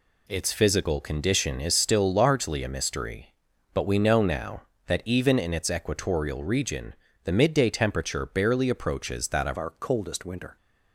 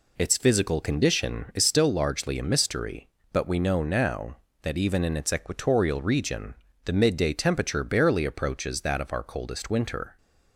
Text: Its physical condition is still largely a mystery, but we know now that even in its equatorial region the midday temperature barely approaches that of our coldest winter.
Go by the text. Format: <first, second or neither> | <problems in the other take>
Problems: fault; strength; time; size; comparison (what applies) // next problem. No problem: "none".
second | pauses between "region" and "the"; slight; at 6.9 s; 0.28 s long; slight in the second // changes voice at "our"; from 9.5 s on; 1.0 s long